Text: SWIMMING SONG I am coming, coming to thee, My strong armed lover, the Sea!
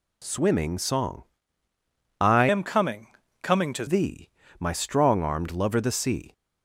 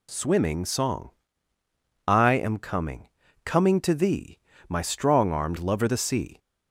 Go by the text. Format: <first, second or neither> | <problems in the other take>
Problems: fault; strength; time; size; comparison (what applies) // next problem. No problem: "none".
second | pauses between "SONG" and "I"; noticeable; at 1.2 s; 0.96 s long; noticeable in the second // changes voice from "am" to "to"; from 2.4 to 3.8 s; 1.4 s long